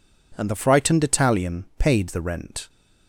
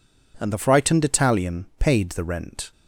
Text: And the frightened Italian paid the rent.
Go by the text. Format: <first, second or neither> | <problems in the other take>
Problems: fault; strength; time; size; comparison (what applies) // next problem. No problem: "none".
neither | none